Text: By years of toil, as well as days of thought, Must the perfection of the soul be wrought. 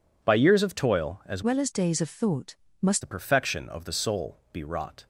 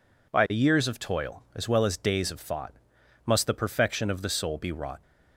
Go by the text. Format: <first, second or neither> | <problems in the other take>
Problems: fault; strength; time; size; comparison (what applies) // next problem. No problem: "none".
second | changes voice from "well" to "Must"; from 1.4 to 3.0 s; 1.6 s long // pauses between "soul" and "be"; slight; at 4.3 s; 0.16 s long